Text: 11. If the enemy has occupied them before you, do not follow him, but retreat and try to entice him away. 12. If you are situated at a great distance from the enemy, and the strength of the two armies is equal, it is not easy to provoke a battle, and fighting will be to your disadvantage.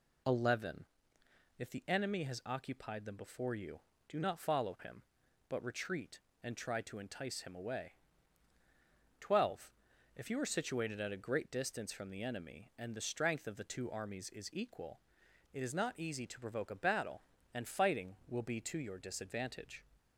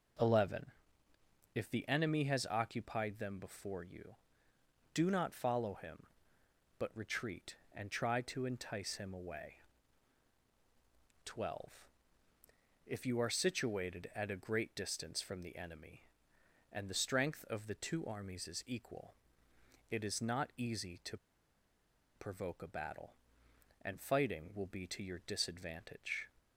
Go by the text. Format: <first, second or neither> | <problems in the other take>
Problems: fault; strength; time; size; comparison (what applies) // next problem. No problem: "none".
first | pauses between "to" and "provoke"; at 21.1 s; 0.99 s long